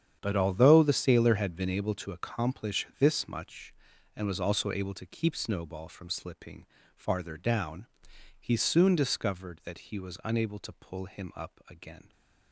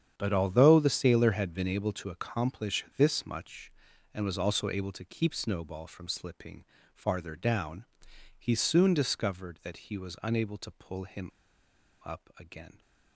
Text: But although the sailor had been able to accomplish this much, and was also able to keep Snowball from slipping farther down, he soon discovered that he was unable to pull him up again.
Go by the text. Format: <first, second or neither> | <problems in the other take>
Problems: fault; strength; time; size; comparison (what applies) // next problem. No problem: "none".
first | starts louder than the rest; strong; until 1.1 s; 8.5 dB; strong in the first // pauses between "slipping" and "farther"; slight; at 6.6 s; 0.30 s long; slight in the first // pauses between "him" and "up"; noticeable; at 11.3 s; 0.74 s long